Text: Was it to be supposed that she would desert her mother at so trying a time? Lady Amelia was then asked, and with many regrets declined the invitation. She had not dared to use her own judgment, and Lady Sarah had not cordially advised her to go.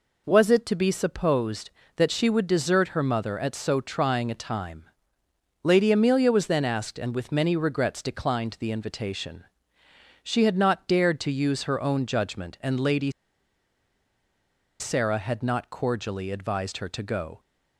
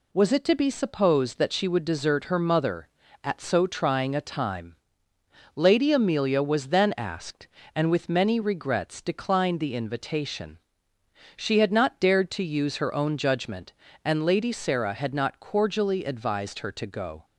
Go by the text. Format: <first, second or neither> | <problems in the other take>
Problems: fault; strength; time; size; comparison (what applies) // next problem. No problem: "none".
second | pauses between "Lady" and "Sarah"; strong; at 13.0 s; 1.7 s long